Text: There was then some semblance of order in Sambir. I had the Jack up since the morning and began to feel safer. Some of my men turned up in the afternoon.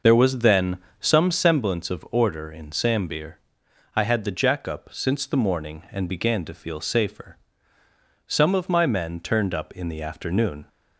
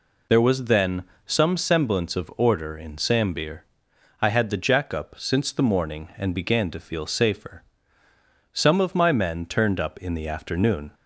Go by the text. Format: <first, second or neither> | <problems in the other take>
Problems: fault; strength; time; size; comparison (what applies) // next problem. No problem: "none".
second | starts louder than the rest; noticeable; until 1.6 s; 6 dB // pauses between "then" and "some"; slight; at 0.7 s; 0.22 s long; slight in the second